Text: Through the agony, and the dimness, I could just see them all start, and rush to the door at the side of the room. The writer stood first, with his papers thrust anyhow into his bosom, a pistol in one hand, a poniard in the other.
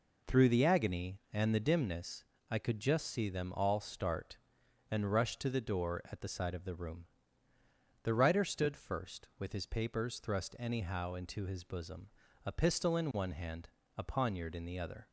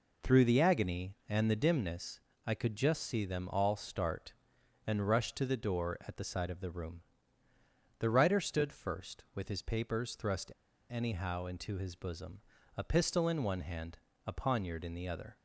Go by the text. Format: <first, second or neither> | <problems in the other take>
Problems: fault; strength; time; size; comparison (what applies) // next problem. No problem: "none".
first | pauses between "thrust" and "anyhow"; at 10.5 s; 0.37 s long